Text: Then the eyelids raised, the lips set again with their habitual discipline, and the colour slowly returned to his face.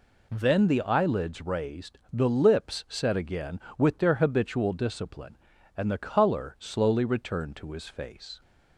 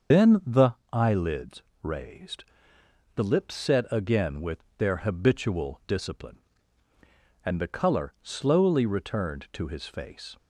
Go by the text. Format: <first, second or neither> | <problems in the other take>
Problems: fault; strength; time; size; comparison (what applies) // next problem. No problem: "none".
first | loses the start of "Then"; at 0.1 s; 90 ms // starts louder than the rest; until 1.3 s; 6.5 dB // pauses between "the" and "eyelids"; slight; at 0.7 s; 0.18 s long // pauses between "eyelids" and "raised"; slight; at 1.6 s; 0.22 s long // pauses between "with" and "their"; slight; at 4.5 s; 0.22 s long